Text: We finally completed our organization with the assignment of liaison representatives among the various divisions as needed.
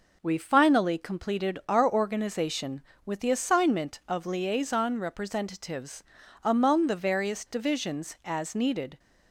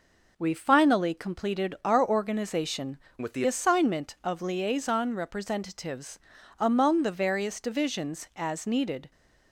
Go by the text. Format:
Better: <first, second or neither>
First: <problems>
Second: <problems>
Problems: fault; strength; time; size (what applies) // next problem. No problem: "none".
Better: first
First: pauses between "representatives" and "among"; at 6.0 s; 0.40 s long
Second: changes voice from "with" to "the"; from 3.2 to 3.4 s; 0.2 s long // pauses between "representatives" and "among"; at 6.1 s; 0.40 s long